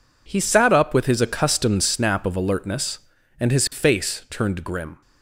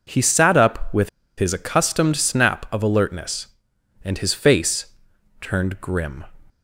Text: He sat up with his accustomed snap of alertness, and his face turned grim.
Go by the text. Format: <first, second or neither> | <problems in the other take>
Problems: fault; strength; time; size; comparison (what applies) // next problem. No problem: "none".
first | pauses between "with" and "his"; slight; at 1.0 s; 0.28 s long // pauses between "face" and "turned"; noticeable; at 4.9 s; 0.48 s long